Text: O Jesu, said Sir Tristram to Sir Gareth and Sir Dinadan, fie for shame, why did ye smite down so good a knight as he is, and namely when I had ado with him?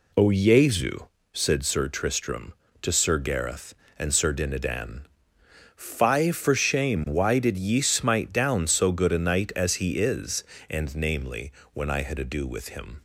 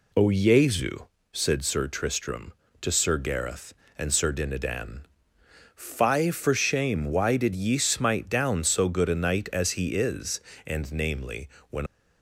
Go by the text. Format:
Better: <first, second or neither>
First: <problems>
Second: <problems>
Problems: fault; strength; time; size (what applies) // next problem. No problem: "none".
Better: first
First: pauses between "namely" and "when"; slight; at 11.5 s; 0.22 s long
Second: pauses between "namely" and "when"; slight; at 11.4 s; 0.22 s long // stops before "I had ado with him"; at 11.8 s